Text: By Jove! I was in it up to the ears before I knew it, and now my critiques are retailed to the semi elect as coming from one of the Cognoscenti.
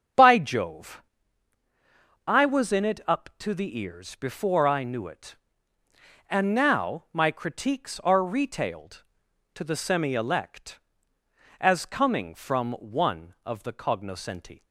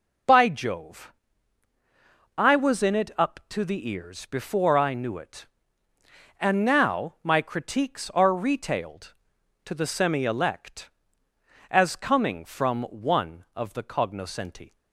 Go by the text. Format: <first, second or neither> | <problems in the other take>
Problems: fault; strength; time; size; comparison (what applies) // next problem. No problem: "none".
second | starts louder than the rest; strong; until 1.2 s; 7.5 dB